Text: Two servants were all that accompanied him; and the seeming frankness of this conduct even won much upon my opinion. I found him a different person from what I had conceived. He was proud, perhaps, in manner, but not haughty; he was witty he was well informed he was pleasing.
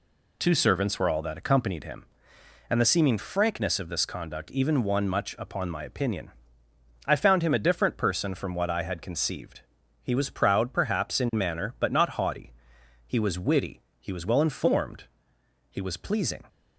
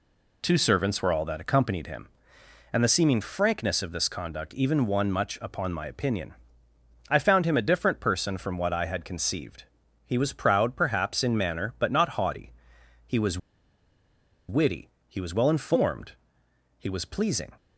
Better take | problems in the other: first | pauses between "was" and "witty"; at 13.3 s; 1.1 s long // pauses between "witty" and "he"; slight; at 14.8 s; 0.18 s long; slight in the first // pauses between "informed" and "he"; noticeable; at 16.1 s; 0.62 s long; noticeable in the first

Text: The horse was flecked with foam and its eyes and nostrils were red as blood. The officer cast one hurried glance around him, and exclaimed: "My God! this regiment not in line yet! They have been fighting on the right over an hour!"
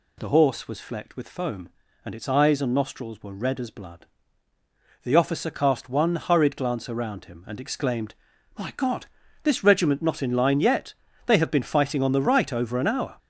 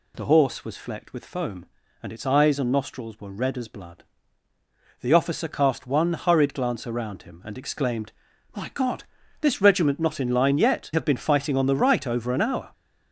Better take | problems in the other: first | skips "They"; at 10.9 s

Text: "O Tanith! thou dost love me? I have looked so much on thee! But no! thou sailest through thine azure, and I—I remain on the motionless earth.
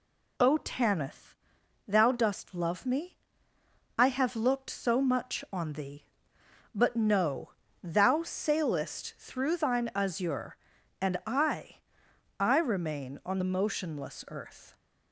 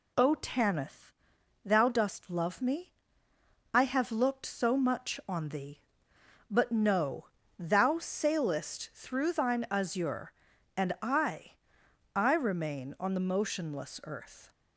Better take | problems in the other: neither | none

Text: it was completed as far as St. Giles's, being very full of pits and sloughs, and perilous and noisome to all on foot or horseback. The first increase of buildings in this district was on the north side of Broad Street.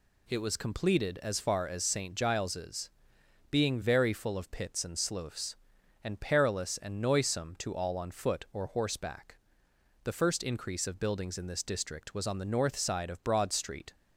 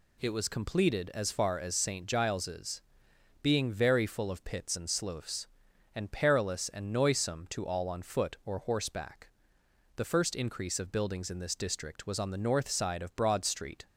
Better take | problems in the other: neither | none

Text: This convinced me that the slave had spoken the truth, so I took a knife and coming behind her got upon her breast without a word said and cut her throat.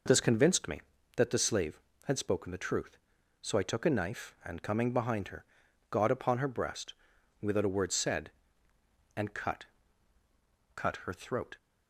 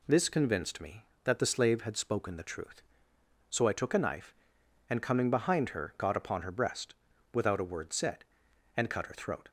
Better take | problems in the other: second | pauses between "her" and "got"; noticeable; at 5.4 s; 0.48 s long // pauses between "breast" and "without"; noticeable; at 6.9 s; 0.50 s long; also in the second // says "cut" twice; at 10.7 s

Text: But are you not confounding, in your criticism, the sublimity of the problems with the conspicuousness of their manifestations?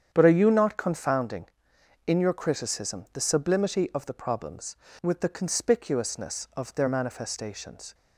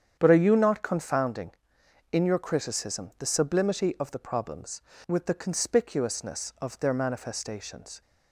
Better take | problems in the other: neither | starts louder than the rest; strong; the same in both

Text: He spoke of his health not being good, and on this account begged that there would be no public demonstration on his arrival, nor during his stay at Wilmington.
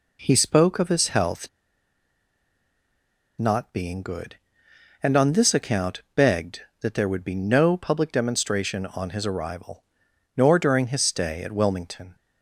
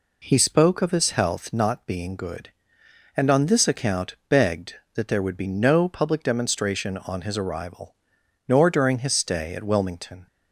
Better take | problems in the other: second | pauses between "health" and "not"; strong; at 1.4 s; 1.8 s long

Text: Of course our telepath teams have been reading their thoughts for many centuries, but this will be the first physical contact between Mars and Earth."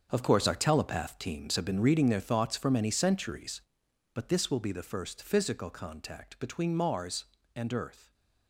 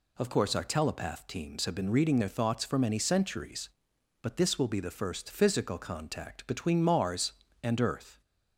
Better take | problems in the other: second | gets quieter; strong; throughout; 12.5 dB

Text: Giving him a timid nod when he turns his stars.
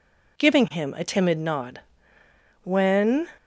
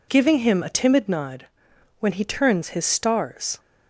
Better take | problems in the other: second | pauses between "nod" and "when"; noticeable; at 1.7 s; 0.82 s long; noticeable in the second // stops before "he turns his stars"; at 3.3 s

